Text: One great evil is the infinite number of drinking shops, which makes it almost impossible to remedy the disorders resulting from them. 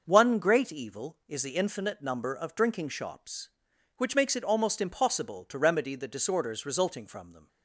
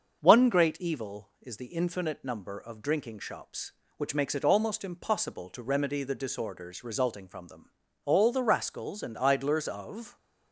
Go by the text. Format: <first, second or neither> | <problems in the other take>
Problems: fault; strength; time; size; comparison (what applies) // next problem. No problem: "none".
first | starts louder than the rest; until 1.2 s; 6.5 dB; noticeable in the first // goes on to say "All the rascals and idlers of"; strong; from 8.0 s on; 2.1 s long